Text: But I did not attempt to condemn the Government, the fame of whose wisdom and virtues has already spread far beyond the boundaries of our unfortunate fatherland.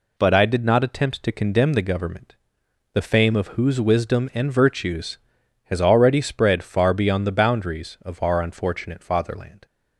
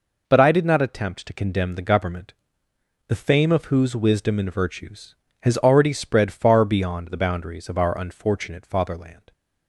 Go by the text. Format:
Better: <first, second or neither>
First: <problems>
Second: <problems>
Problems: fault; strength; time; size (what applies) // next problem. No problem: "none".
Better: neither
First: none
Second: none